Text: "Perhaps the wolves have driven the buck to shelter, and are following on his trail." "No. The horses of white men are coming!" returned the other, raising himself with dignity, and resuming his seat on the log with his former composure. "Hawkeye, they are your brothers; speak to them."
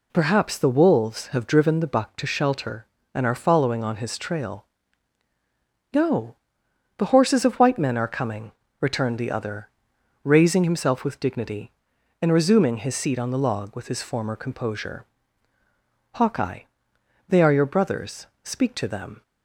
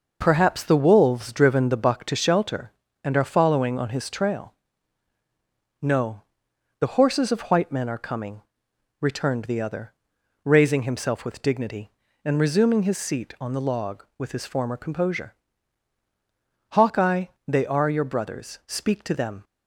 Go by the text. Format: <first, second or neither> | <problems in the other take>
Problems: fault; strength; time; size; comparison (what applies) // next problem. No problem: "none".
first | skips "have"; at 1.3 s